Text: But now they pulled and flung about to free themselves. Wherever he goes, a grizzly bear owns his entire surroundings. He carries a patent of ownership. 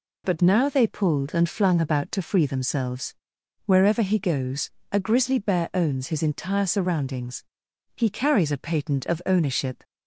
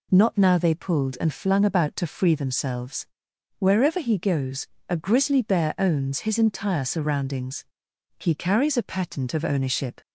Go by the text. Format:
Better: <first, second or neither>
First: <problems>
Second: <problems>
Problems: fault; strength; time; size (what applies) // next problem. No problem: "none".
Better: first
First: none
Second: says "Not" for "But"; at 0.1 s